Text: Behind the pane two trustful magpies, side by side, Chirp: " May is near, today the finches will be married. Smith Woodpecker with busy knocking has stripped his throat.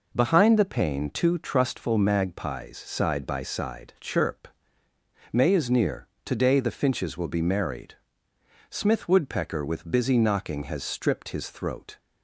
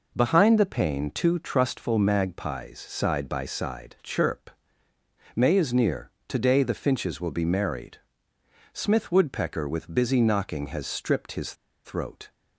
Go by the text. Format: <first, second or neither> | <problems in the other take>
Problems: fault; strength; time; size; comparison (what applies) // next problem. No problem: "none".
first | pauses between "his" and "throat"; slight; at 11.5 s; 0.30 s long